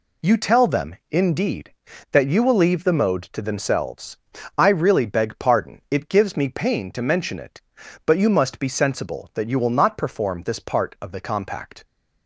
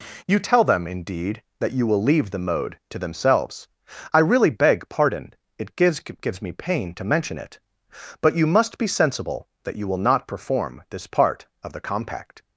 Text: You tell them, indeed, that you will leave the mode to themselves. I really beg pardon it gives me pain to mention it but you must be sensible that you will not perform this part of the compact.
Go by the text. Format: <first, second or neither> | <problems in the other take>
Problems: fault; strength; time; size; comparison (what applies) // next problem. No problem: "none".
first | pauses between "pardon" and "it"; slight; at 5.3 s; 0.26 s long // says "gives" twice; at 5.9 s